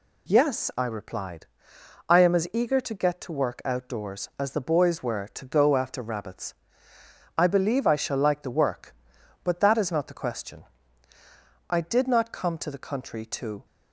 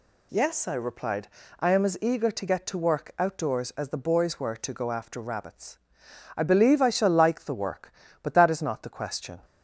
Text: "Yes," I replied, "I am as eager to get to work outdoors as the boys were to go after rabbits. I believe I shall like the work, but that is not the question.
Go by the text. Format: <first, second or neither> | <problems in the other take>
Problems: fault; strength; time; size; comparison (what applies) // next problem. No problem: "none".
second | goes on to say "I did not come to the country to"; strong; from 11.6 s on; 1.9 s long